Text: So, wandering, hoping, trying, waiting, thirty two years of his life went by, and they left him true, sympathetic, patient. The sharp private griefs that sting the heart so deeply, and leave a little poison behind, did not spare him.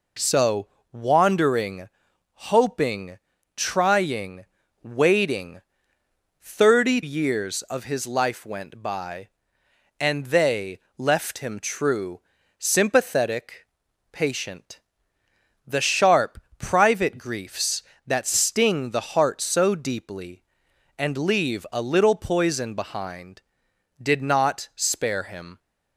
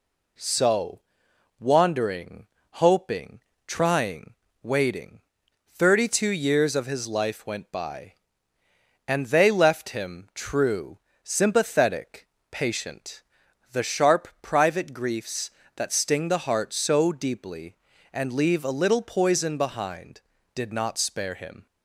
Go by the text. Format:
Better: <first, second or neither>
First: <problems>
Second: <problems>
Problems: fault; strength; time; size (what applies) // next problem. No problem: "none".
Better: second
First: skips "two"; at 7.0 s // pauses between "they" and "left"; slight; at 10.7 s; 0.18 s long // pauses between "sharp" and "private"; slight; at 16.4 s; 0.18 s long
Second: none